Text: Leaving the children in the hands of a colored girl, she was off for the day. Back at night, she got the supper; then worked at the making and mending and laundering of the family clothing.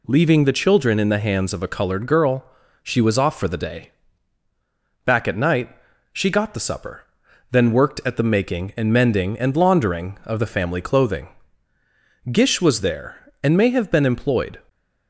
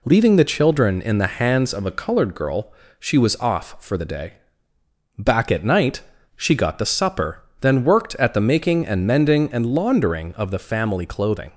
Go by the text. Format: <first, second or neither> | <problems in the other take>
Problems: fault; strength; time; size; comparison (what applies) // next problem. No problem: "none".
second | goes on to say "Gish was there and may have been employed"; strong; from 12.3 s on; 2.2 s long